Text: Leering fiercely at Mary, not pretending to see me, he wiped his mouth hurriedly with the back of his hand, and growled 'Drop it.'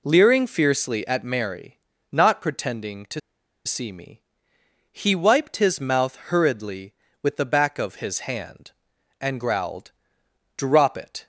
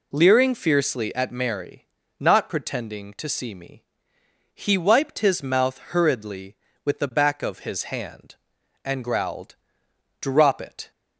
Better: second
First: pauses between "to" and "see"; noticeable; at 3.1 s; 0.46 s long // pauses between "growled" and "Drop"; noticeable; at 9.9 s; 0.66 s long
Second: pauses between "growled" and "Drop"; noticeable; at 9.5 s; 0.66 s long

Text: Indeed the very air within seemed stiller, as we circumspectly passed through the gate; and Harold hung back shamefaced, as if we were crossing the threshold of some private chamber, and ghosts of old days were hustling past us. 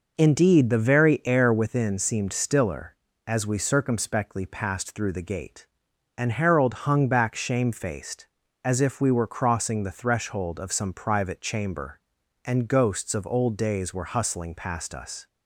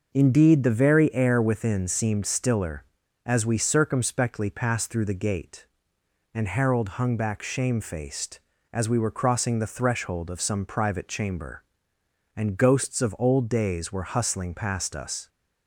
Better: first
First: none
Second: skips "if"; at 8.8 s

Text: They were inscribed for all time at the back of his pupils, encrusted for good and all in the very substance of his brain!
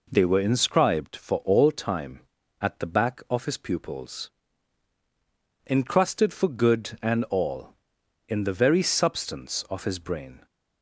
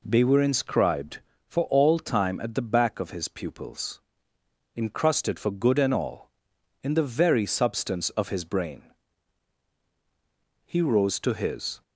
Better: first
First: none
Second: goes on to say "He rose to his"; noticeable; from 10.6 s on; 1.1 s long

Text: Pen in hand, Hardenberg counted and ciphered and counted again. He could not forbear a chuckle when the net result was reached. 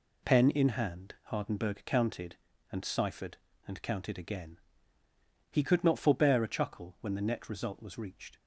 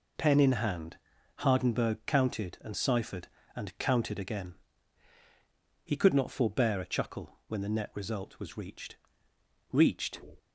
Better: first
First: none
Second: says "reached" twice; at 9.7 s

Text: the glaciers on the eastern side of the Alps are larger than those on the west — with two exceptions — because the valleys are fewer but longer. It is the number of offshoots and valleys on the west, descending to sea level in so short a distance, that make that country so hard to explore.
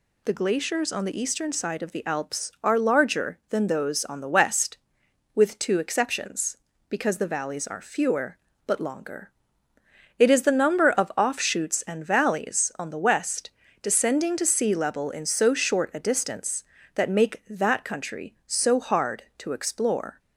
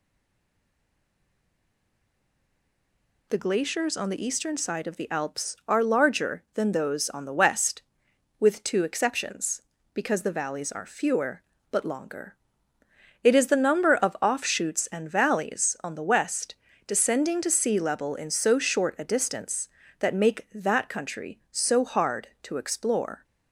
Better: first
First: none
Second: stays silent before the first word; strong; until 3.2 s; 3.2 s long

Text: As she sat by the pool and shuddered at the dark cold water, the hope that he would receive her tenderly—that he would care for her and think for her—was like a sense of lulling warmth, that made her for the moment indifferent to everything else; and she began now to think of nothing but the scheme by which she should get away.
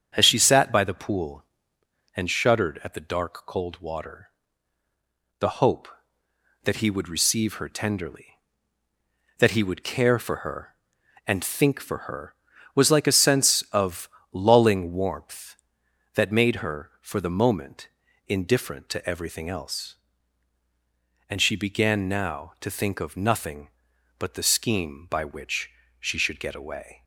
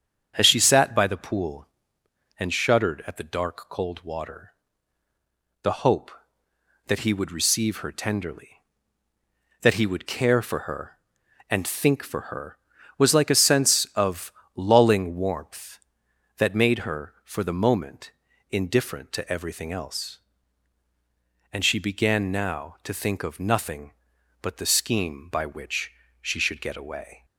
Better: neither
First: starts louder than the rest; strong; until 1.1 s; 8 dB // pauses between "of" and "lulling"; slight; at 14.0 s; 0.22 s long // pauses between "moment" and "indifferent"; at 17.8 s; 0.40 s long // pauses between "which" and "she"; slight; at 25.6 s; 0.32 s long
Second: starts louder than the rest; strong; until 1.3 s; 8 dB // pauses between "of" and "lulling"; slight; at 14.3 s; 0.22 s long // pauses between "moment" and "indifferent"; at 18.1 s; 0.40 s long // pauses between "which" and "she"; slight; at 25.9 s; 0.32 s long

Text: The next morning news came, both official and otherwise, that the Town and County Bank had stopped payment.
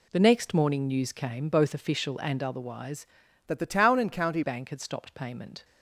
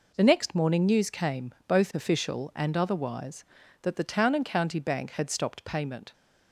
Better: second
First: changes voice from "that" to "County"; from 3.4 to 4.4 s; 1.0 s long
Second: none

